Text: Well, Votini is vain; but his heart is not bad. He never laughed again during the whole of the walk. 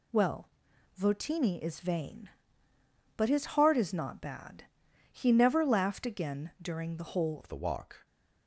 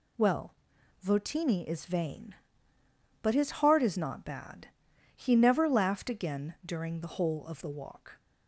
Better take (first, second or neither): second